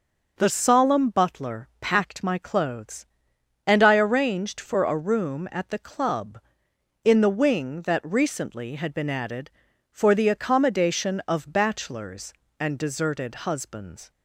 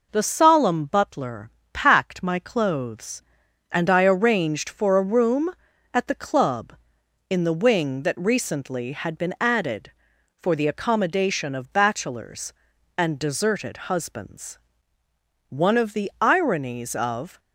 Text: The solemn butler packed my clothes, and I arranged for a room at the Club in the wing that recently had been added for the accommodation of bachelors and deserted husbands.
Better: first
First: none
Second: pauses between "butler" and "packed"; slight; at 1.5 s; 0.24 s long // goes on to say "One of the ironies of"; strong; from 15.5 s on; 1.8 s long

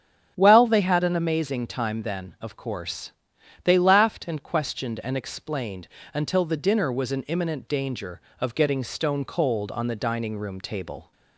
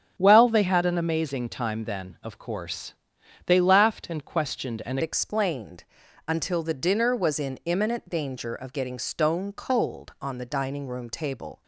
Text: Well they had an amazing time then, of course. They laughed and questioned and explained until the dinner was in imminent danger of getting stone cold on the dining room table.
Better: first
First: starts louder than the rest; strong; until 1.3 s; 8 dB // pauses between "explained" and "until"; slight; at 5.8 s; 0.26 s long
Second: starts louder than the rest; strong; until 1.1 s; 7.5 dB // changes voice at "explained"; from 5.0 s on; 6.6 s long // pauses between "explained" and "until"; at 5.8 s; 0.42 s long

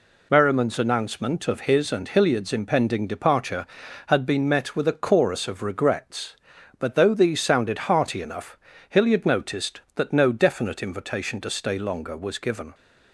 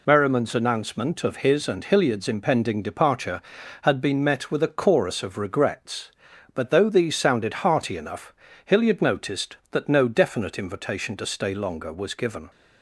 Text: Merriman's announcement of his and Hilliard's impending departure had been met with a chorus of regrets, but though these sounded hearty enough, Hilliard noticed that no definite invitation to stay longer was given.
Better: neither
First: none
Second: none

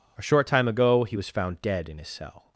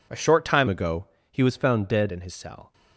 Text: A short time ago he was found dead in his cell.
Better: first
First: none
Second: changes voice from "ago" to "dead"; from 0.6 to 2.1 s; 1.5 s long // pauses between "ago" and "he"; slight; at 1.0 s; 0.26 s long

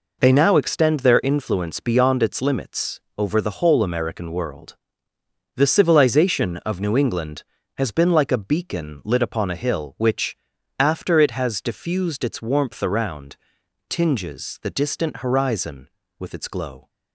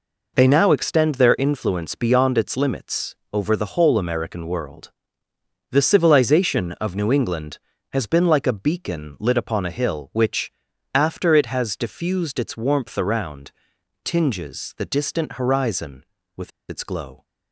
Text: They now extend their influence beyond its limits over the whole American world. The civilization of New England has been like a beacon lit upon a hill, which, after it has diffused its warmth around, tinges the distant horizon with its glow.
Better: first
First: pauses between "limits" and "over"; slight; at 2.9 s; 0.18 s long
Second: pauses between "limits" and "over"; slight; at 3.1 s; 0.18 s long // pauses between "with" and "its"; slight; at 16.4 s; 0.19 s long

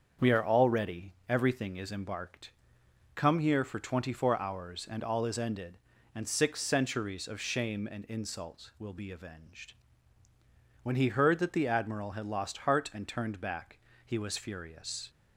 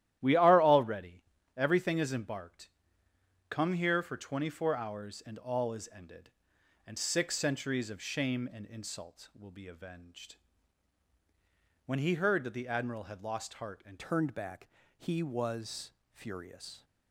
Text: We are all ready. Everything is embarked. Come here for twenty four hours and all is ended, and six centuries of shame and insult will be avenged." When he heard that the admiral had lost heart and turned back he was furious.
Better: first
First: starts louder than the rest; until 1.3 s; 7 dB // pauses between "back" and "he"; slight; at 13.7 s; 0.26 s long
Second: starts louder than the rest; strong; until 1.2 s; 12.5 dB // changes voice at "turned"; from 13.9 s on; 2.9 s long // pauses between "back" and "he"; slight; at 14.6 s; 0.28 s long // pauses between "was" and "furious"; slight; at 15.8 s; 0.24 s long

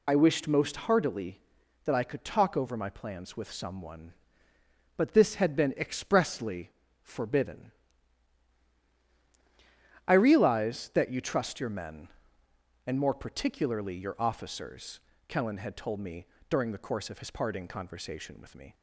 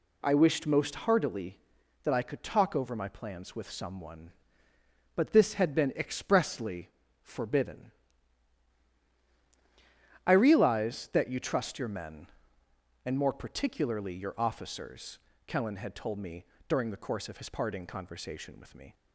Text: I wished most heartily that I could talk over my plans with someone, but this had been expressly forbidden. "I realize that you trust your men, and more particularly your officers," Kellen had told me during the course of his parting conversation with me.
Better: second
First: loses the start of "I"; at 0.0 s; 40 ms // pauses between "expressly" and "forbidden"; slight; at 6.7 s; 0.30 s long // pauses between "me" and "during"; slight; at 16.2 s; 0.22 s long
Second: pauses between "expressly" and "forbidden"; slight; at 6.9 s; 0.32 s long // pauses between "me" and "during"; slight; at 16.4 s; 0.22 s long

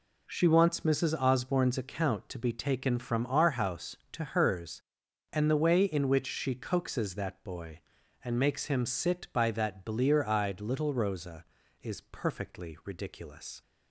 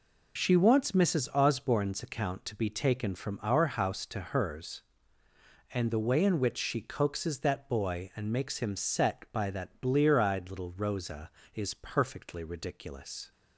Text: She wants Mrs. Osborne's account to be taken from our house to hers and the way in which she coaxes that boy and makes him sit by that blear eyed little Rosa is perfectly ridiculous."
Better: first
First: none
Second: says "set" for "sit"; at 8.7 s

